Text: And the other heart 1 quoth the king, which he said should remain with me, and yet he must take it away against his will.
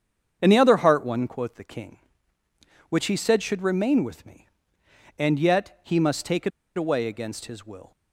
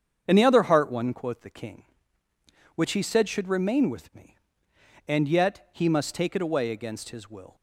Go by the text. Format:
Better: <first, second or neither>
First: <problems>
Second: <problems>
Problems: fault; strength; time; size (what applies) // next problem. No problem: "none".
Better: second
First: starts louder than the rest; strong; until 1.4 s; 7.5 dB // pauses between "it" and "away"; slight; at 6.5 s; 0.26 s long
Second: starts louder than the rest; strong; until 1.2 s; 7.5 dB